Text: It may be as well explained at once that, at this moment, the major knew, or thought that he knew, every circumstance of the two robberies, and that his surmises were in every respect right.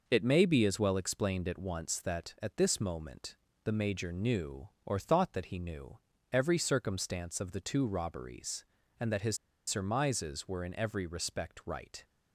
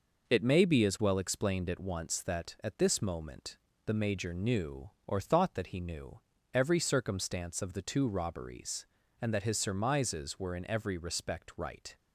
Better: second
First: pauses between "his" and "surmises"; slight; at 9.3 s; 0.31 s long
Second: none

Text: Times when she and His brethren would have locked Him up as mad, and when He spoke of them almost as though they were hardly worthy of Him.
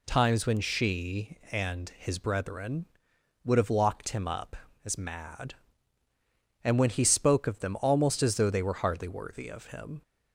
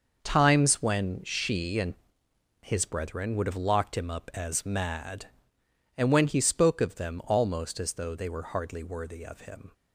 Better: first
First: none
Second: gets quieter; strong; throughout; 10 dB // pauses between "and" and "His"; noticeable; at 1.9 s; 0.66 s long

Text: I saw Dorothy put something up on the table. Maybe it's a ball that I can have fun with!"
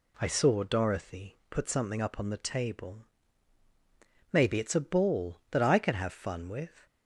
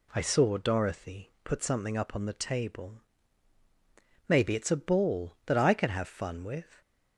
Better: neither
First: none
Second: none

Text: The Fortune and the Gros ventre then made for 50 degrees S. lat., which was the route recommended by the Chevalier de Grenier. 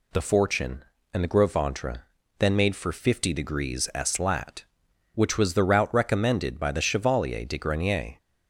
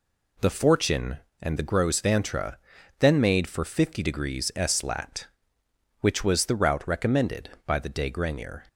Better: first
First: pauses between "ventre" and "then"; slight; at 2.0 s; 0.36 s long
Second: pauses between "ventre" and "then"; at 2.5 s; 0.42 s long // skips "Chevalier"; at 7.8 s

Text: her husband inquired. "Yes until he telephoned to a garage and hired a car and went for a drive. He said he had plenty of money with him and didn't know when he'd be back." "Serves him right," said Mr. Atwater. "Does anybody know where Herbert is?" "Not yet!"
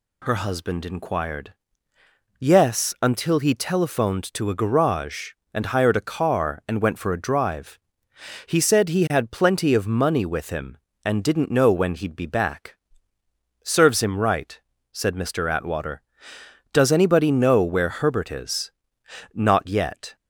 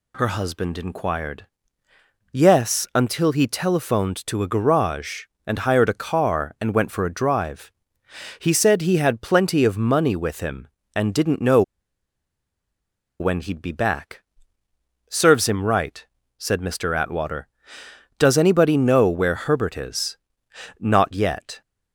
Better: first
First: none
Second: pauses between "know" and "when"; strong; at 11.6 s; 1.5 s long

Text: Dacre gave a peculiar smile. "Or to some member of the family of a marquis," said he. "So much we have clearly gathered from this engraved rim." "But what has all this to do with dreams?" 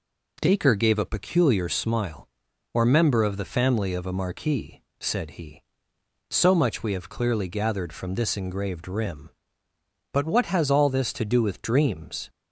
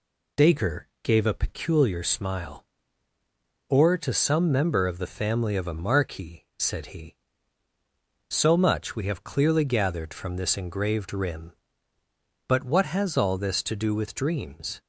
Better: second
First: skips "to some"; at 2.8 s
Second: none

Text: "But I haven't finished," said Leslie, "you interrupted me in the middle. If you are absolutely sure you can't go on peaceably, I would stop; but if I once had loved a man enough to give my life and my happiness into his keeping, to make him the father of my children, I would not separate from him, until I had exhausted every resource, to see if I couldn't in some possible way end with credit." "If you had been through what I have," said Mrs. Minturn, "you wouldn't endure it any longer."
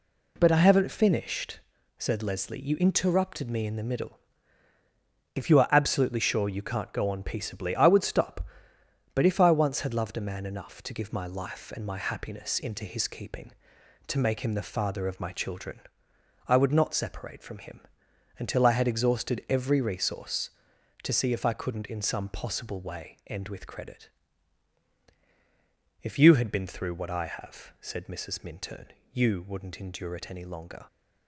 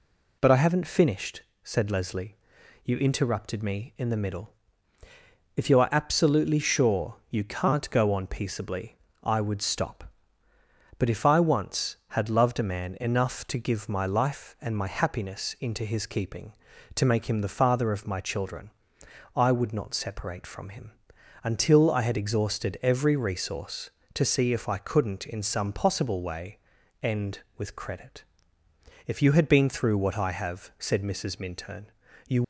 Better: first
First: none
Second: pauses between "way" and "end"; at 26.5 s; 0.44 s long // stops before "wouldn't endure it any longer"; at 32.4 s

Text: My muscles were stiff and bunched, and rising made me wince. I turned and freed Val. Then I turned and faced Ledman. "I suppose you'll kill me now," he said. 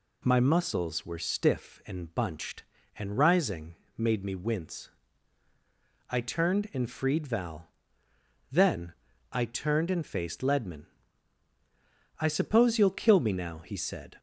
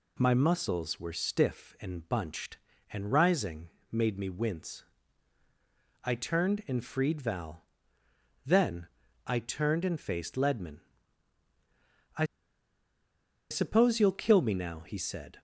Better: first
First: pauses between "rising" and "made"; slight; at 3.7 s; 0.22 s long // pauses between "Then" and "I"; at 8.9 s; 0.40 s long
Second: pauses between "rising" and "made"; slight; at 3.6 s; 0.22 s long // pauses between "Then" and "I"; at 8.8 s; 0.40 s long // pauses between "I" and "suppose"; strong; at 12.2 s; 1.2 s long

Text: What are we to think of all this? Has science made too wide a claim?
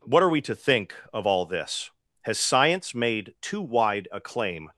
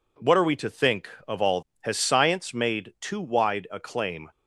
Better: first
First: none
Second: skips "this"; at 1.7 s

